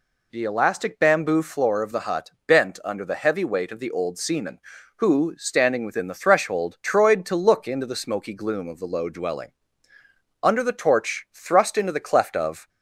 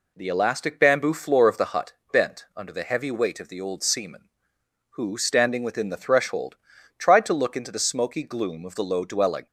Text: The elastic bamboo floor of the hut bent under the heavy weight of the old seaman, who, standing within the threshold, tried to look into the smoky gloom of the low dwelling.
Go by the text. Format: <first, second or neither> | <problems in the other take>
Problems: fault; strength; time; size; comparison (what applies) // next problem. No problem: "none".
second | pauses between "hut" and "bent"; slight; at 2.3 s; 0.16 s long; slight in the second // goes on to say "Under the torch thrust into the cleft of"; strong; from 10.4 s on; 2.2 s long